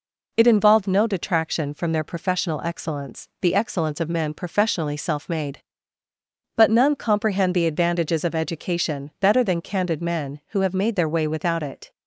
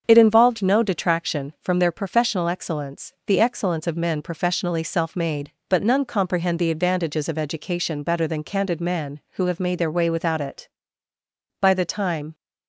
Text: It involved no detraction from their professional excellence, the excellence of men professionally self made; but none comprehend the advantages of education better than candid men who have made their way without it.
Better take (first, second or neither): first